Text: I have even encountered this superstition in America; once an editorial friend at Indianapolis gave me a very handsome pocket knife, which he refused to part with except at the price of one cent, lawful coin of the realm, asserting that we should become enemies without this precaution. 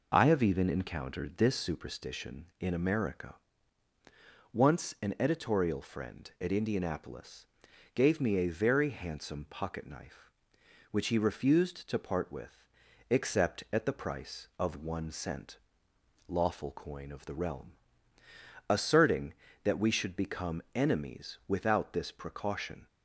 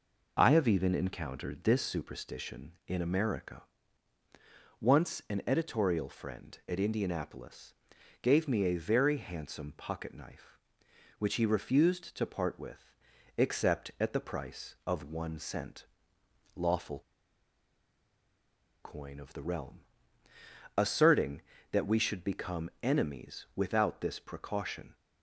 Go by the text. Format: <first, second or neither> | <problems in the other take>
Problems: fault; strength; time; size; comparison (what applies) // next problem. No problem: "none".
first | pauses between "Indianapolis" and "gave"; noticeable; at 7.7 s; 0.48 s long; noticeable in the first // pauses between "with" and "except"; at 12.9 s; 0.42 s long; also in the first // pauses between "lawful" and "coin"; strong; at 17.0 s; 1.8 s long